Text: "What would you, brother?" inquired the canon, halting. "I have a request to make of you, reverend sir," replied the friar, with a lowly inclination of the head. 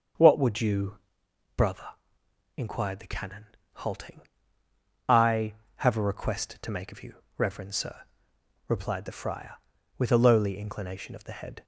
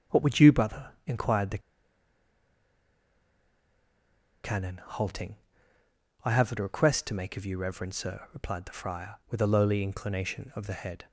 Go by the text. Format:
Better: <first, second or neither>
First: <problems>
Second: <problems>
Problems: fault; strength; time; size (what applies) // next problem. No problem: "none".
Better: first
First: starts louder than the rest; until 1.7 s; 6.5 dB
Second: starts louder than the rest; strong; until 1.2 s; 8 dB // pauses between "the" and "canon"; strong; at 1.5 s; 2.8 s long